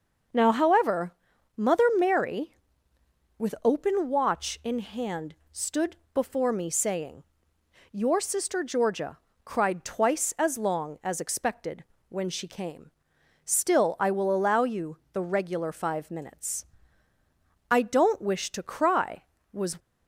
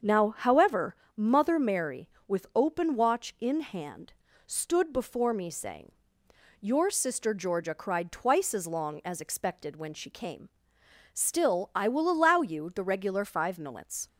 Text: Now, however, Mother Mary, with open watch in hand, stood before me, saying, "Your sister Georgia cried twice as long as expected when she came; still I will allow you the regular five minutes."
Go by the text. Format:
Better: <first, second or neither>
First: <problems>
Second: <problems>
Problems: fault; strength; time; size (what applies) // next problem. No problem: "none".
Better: second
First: starts louder than the rest; noticeable; until 1.7 s; 6 dB // pauses between "stood" and "before"; slight; at 5.9 s; 0.18 s long // pauses between "Georgia" and "cried"; slight; at 9.1 s; 0.26 s long // pauses between "expected" and "when"; slight; at 11.8 s; 0.26 s long // goes on to say "I don't wish to cry was"; strong; from 17.6 s on; 2.1 s long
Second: starts louder than the rest; until 1.2 s; 7 dB